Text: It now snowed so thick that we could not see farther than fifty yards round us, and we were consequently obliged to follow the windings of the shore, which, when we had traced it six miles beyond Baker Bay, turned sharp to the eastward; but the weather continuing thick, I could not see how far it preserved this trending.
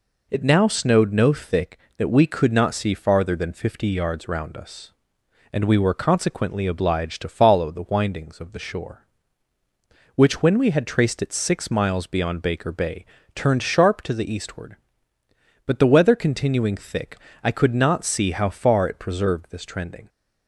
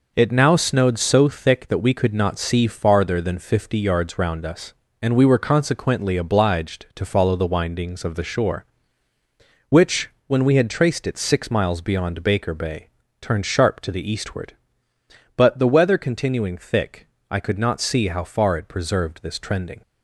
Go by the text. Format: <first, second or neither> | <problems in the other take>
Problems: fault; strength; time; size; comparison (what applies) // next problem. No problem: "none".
second | says "no" for "so"; at 1.1 s